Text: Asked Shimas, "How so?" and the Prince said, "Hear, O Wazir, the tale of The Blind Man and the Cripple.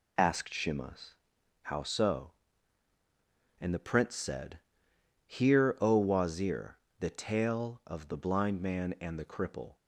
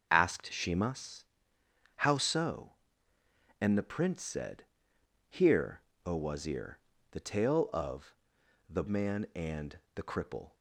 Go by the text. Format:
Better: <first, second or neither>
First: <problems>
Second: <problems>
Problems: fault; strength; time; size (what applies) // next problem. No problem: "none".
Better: first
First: none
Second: starts louder than the rest; until 1.1 s; 6 dB // pauses between "of" and "The"; noticeable; at 8.1 s; 0.56 s long // skips "Blind"; at 8.8 s // pauses between "and" and "the"; slight; at 9.7 s; 0.16 s long